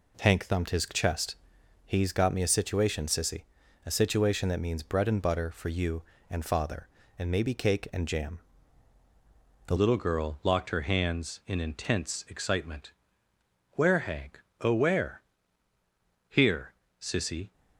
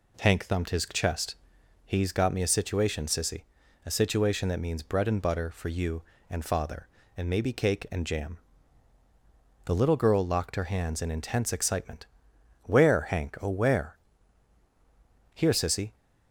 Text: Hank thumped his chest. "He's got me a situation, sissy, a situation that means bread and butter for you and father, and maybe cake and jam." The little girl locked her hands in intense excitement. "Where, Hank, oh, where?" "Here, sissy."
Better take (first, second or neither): second